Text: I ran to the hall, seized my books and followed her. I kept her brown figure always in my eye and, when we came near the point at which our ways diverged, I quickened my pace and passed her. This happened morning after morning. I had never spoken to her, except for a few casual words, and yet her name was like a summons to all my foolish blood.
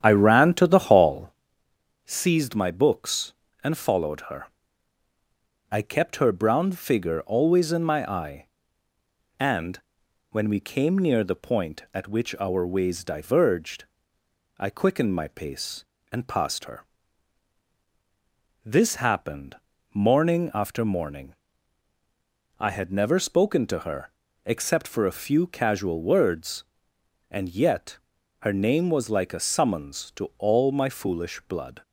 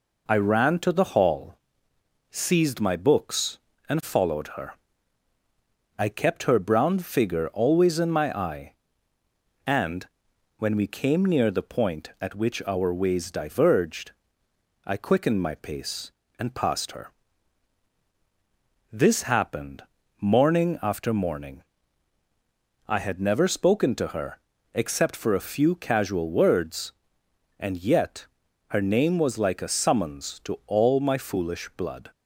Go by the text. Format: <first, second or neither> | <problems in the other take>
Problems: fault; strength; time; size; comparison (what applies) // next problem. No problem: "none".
second | starts louder than the rest; strong; until 1.5 s; 9.5 dB // pauses between "happened" and "morning"; slight; at 19.5 s; 0.36 s long; slight in the second // pauses between "yet" and "her"; at 27.9 s; 0.44 s long; also in the second